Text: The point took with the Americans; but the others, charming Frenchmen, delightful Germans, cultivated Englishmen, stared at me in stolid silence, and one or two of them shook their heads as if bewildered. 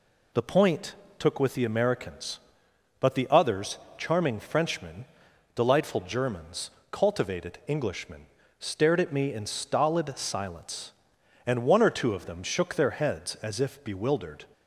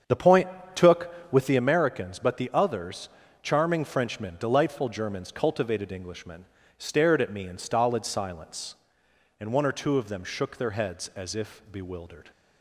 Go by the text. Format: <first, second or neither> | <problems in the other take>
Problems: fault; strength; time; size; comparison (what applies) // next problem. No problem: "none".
first | starts louder than the rest; strong; until 1.7 s; 7.5 dB // pauses between "point" and "took"; slight; at 0.4 s; 0.26 s long; slight in the first